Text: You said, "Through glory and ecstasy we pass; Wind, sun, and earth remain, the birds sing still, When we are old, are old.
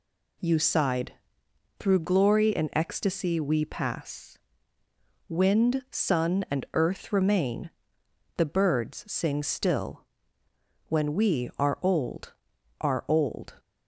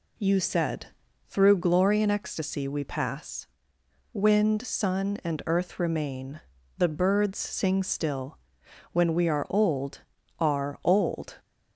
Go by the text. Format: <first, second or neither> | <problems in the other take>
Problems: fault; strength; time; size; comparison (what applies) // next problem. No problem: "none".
second | says "sighed" for "said"; at 0.5 s